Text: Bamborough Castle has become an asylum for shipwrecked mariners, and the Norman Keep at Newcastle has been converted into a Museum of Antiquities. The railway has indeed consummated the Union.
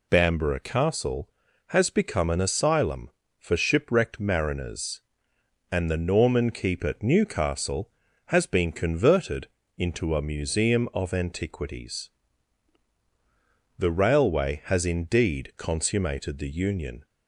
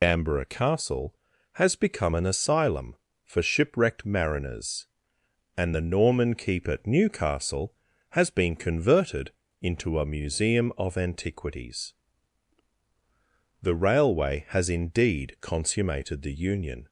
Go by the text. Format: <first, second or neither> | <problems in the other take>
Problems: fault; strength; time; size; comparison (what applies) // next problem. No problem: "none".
first | loses the start of "Bamborough"; at 0.0 s; 60 ms // pauses between "converted" and "into"; slight; at 9.3 s; 0.30 s long; slight in the first